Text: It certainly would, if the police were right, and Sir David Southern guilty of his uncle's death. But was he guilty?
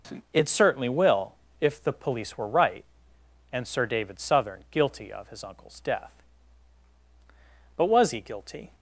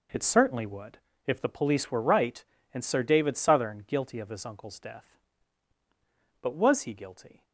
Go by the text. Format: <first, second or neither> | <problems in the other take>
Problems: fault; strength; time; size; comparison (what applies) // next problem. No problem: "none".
second | says "will" for "would"; at 0.8 s